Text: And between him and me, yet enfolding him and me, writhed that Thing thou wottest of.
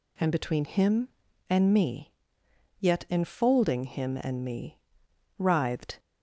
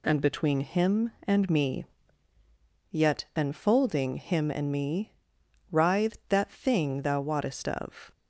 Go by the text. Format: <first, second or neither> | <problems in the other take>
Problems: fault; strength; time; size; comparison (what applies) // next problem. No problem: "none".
second | stops before "that Thing thou wottest of"; at 5.9 s